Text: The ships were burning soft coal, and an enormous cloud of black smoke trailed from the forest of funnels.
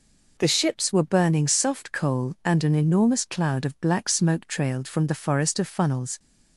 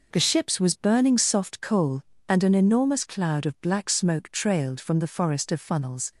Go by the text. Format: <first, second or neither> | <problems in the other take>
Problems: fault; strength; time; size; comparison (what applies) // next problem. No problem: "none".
first | says "was" for "were"; at 0.5 s